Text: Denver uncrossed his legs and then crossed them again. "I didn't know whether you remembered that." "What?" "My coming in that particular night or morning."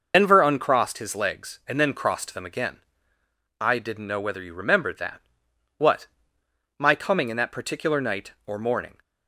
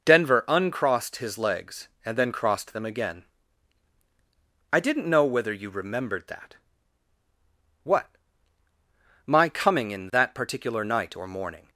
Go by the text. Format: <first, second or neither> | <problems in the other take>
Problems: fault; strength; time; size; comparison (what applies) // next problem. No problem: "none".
second | loses the start of "Denver"; at 0.1 s; 65 ms